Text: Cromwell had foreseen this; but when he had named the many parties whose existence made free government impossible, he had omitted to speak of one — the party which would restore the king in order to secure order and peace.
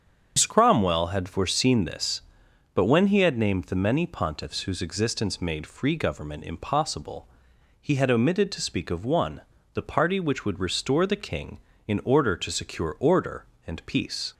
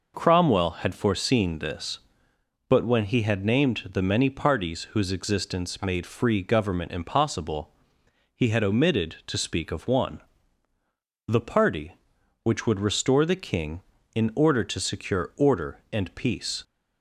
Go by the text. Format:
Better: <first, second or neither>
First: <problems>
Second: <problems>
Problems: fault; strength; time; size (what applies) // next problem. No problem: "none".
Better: second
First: starts louder than the rest; until 1.4 s; 7 dB // says "pontiffs" for "parties"; at 4.0 s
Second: none